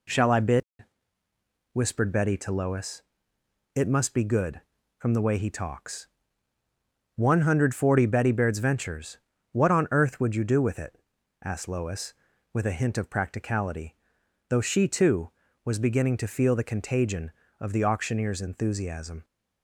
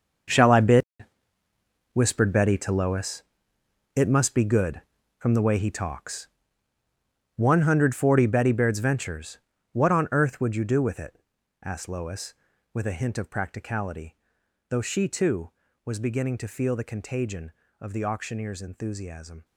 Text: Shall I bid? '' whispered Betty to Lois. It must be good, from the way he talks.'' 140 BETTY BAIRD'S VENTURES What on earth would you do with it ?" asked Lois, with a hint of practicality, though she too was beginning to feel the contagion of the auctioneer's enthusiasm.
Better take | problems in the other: first | gets quieter; noticeable; throughout; 4.5 dB // pauses between "VENTURES" and "What"; slight; at 9.3 s; 0.34 s long; slight in the first

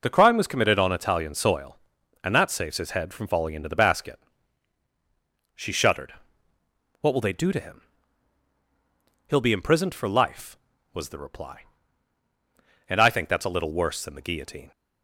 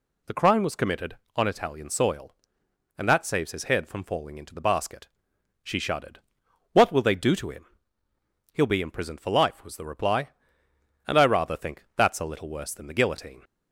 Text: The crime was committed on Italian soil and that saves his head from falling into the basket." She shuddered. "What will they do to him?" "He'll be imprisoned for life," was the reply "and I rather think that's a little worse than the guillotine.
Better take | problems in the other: second | skips "rather"; at 13.0 s

